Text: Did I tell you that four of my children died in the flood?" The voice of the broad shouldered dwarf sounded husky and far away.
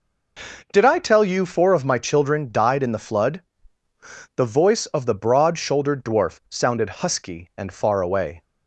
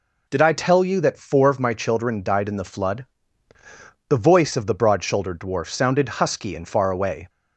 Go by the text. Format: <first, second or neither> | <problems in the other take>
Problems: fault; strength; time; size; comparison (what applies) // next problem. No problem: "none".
second | skips "that"; at 1.4 s